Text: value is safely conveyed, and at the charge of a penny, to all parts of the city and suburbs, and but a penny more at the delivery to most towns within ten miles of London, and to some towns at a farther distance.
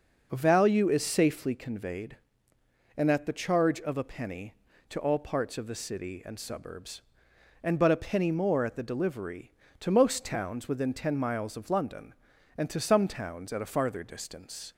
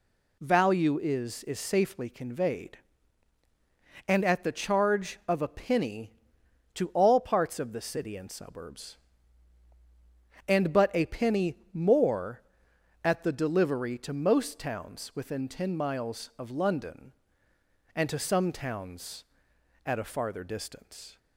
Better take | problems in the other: first | says "is" twice; at 1.4 s // pauses between "penny" and "more"; slight; at 11.5 s; 0.16 s long

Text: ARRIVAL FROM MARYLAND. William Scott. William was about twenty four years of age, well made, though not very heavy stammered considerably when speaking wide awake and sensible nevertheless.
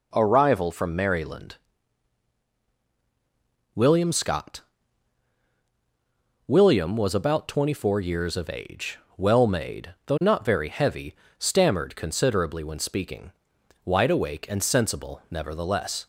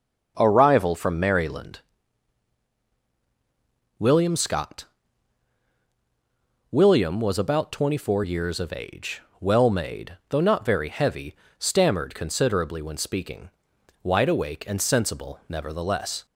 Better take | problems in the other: first | starts louder than the rest; until 1.7 s; 6.5 dB // pauses between "heavy" and "stammered"; slight; at 11.3 s; 0.22 s long; slight in the first // pauses between "speaking" and "wide"; noticeable; at 13.5 s; 0.50 s long; noticeable in the first

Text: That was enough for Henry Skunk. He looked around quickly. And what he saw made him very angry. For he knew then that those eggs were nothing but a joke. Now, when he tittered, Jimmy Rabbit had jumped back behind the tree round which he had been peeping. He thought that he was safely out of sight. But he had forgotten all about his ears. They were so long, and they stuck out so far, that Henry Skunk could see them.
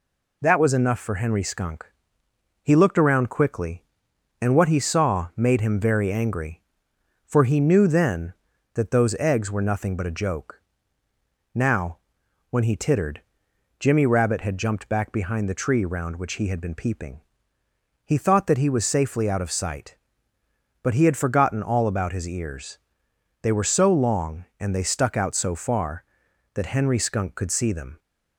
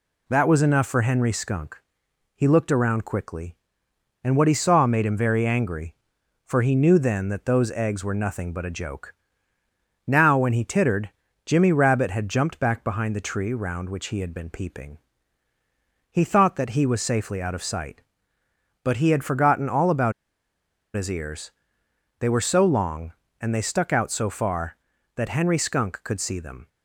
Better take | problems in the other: first | pauses between "about" and "his"; noticeable; at 20.1 s; 0.83 s long

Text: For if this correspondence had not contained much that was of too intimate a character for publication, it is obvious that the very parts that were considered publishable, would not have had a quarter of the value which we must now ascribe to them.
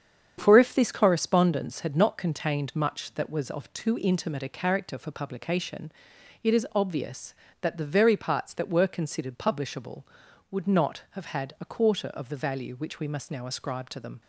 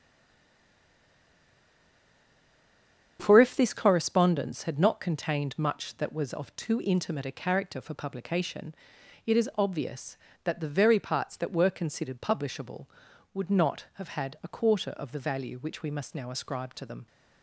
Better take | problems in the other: first | stays silent before the first word; strong; until 3.1 s; 3.1 s long // starts louder than the rest; strong; until 4.2 s; 8 dB; strong in the first

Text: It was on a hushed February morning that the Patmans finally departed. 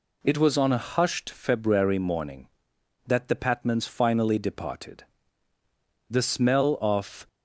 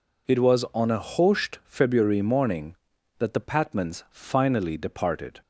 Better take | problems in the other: second | goes on to say "The smell of"; noticeable; from 6.0 s on; 1.1 s long

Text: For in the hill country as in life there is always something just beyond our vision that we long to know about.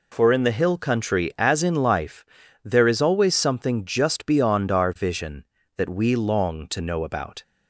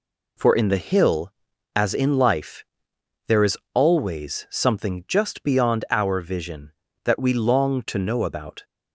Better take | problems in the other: first | skips "country"; at 1.5 s // pauses between "life" and "there"; noticeable; at 2.6 s; 0.62 s long; also in the first // pauses between "is" and "always"; slight; at 3.5 s; 0.16 s long

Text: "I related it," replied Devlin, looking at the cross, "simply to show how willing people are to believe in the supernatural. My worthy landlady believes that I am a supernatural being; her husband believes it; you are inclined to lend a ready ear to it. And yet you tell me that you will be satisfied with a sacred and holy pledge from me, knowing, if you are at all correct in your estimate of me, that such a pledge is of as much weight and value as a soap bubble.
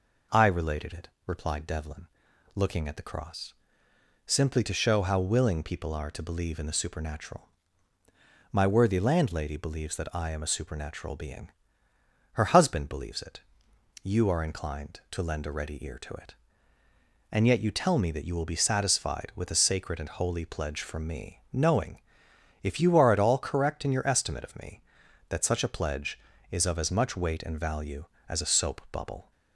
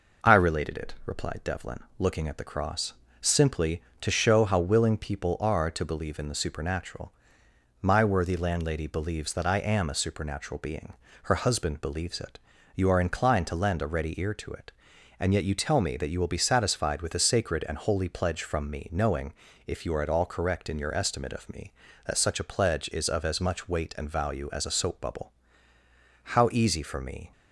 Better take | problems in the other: first | goes on to say "How easy for me"; noticeable; from 26.2 s on; 1.0 s long

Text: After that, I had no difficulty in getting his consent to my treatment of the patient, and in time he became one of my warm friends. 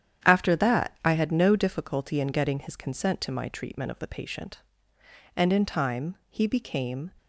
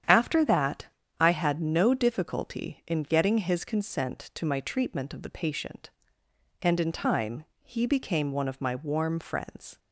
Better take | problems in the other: second | starts louder than the rest; strong; until 1.3 s; 9.5 dB; strong in the second // pauses between "time" and "he"; slight; at 6.1 s; 0.16 s long; slight in the second // stops before "one of my warm friends"; at 7.1 s

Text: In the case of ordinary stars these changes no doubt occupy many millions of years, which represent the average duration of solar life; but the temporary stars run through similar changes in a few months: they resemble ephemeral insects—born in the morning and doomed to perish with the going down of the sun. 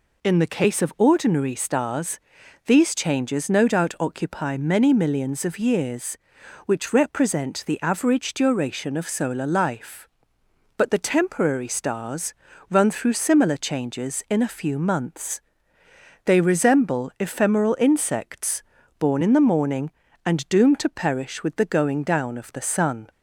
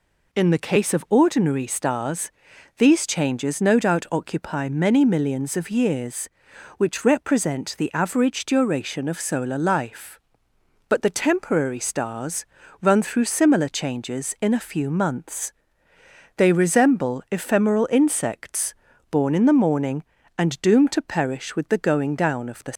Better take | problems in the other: first | pauses between "stars" and "these"; noticeable; at 2.3 s; 0.46 s long; noticeable in the first // pauses between "stars" and "run"; slight; at 12.4 s; 0.36 s long; slight in the first // stops before "sun"; at 22.7 s

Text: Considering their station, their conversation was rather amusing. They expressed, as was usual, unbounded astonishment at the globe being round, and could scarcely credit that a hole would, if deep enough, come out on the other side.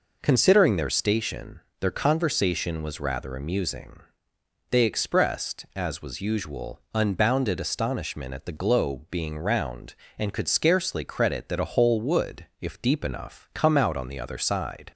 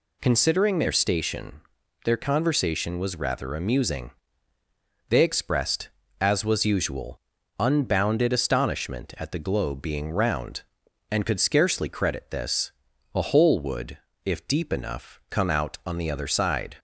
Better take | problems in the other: first | says "this" for "that"; at 12.3 s

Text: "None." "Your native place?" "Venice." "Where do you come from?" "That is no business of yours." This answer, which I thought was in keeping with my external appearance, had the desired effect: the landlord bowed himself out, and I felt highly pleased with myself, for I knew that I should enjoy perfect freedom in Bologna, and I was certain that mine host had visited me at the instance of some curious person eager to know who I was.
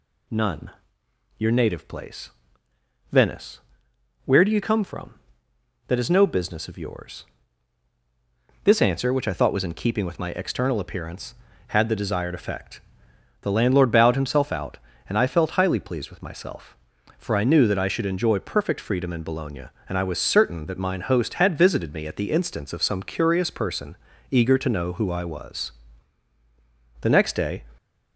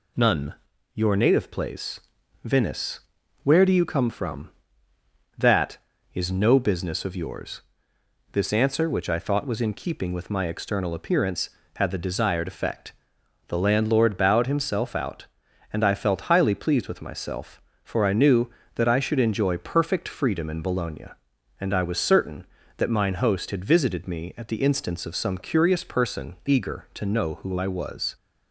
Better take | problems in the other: second | pauses between "person" and "eager"; slight; at 23.9 s; 0.36 s long // goes on to say "The next day"; noticeable; from 27.0 s on; 0.64 s long

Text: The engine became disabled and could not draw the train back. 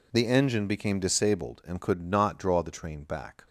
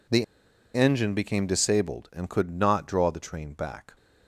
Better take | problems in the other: first | pauses between "The" and "engine"; noticeable; at 0.2 s; 0.49 s long

